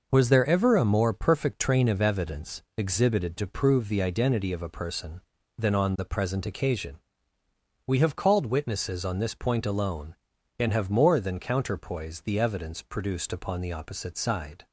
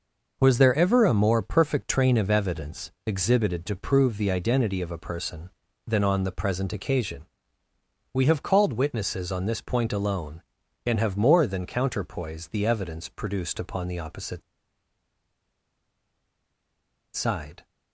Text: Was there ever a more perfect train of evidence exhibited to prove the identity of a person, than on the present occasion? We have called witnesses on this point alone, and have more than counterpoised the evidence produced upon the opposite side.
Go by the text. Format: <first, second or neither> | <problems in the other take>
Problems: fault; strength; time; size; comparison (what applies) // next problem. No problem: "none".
first | pauses between "opposite" and "side"; strong; at 14.4 s; 2.7 s long